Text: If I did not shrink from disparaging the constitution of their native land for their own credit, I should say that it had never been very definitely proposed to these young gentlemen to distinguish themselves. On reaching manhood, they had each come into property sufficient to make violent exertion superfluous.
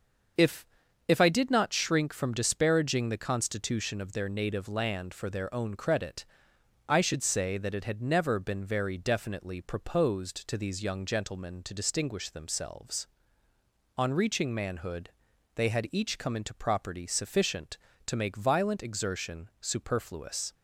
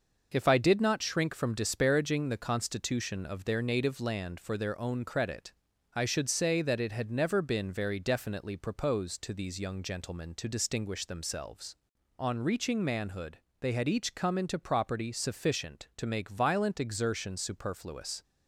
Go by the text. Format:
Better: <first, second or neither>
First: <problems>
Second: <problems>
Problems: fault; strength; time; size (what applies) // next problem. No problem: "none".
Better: second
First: starts louder than the rest; until 1.8 s; 6.5 dB // says "If" twice; at 1.0 s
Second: none